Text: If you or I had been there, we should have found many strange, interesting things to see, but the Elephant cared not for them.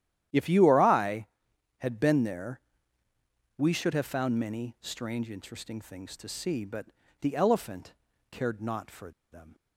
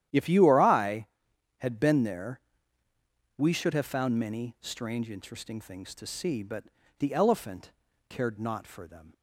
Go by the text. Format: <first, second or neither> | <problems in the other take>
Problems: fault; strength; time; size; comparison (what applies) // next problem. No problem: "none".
second | starts louder than the rest; strong; until 1.8 s; 11 dB; strong in the second // pauses between "but" and "the"; slight; at 6.8 s; 0.34 s long; slight in the second // pauses between "Elephant" and "cared"; at 7.9 s; 0.38 s long; also in the second // pauses between "for" and "them"; slight; at 9.1 s; 0.21 s long